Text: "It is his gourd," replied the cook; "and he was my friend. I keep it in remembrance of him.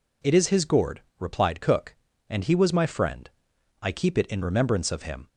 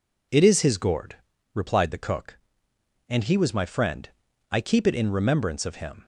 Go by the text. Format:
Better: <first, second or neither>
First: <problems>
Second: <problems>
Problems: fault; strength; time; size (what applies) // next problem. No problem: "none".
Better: second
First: skips "the"; at 1.5 s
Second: none